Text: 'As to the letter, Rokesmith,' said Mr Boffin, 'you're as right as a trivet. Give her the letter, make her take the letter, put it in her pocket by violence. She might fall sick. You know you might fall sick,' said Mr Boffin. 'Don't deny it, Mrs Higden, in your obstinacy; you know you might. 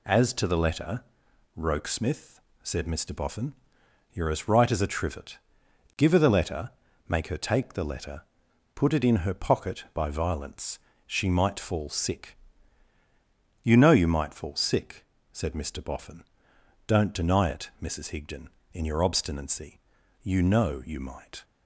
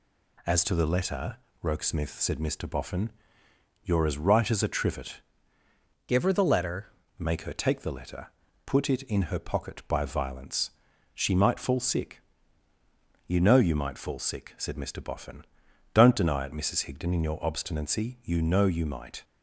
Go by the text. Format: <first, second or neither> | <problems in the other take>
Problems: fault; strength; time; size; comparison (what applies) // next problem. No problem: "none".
first | changes voice from "Give" to "letter"; from 6.0 to 6.8 s; 0.8 s long